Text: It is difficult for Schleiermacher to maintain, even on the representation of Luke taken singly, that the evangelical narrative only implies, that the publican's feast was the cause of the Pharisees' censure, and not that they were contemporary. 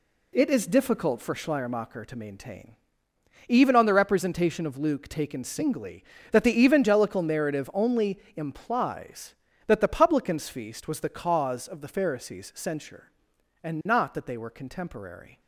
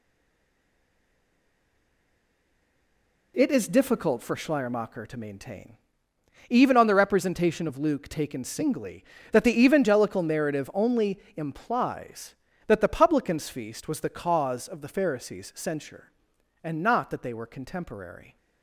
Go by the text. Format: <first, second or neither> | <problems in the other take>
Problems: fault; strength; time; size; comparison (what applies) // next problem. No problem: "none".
first | stays silent before the first word; strong; until 3.3 s; 3.3 s long // pauses between "only" and "implies"; slight; at 11.1 s; 0.18 s long; slight in the first